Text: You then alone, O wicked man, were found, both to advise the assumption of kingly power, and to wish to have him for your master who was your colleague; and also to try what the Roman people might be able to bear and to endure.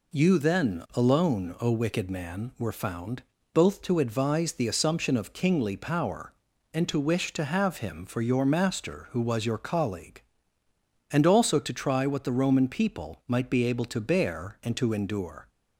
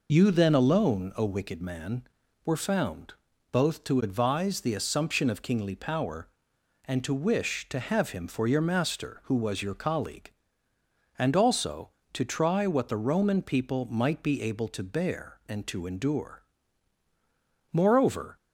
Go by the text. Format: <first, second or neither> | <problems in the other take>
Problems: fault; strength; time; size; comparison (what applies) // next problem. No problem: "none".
first | goes on to say "Moreover"; noticeable; from 17.7 s on; 0.64 s long